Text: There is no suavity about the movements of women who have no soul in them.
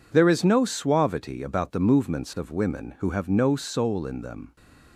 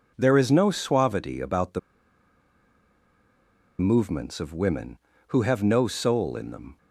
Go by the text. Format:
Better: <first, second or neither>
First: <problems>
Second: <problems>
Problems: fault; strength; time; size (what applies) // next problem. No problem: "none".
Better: first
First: none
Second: pauses between "the" and "movements"; strong; at 1.7 s; 1.9 s long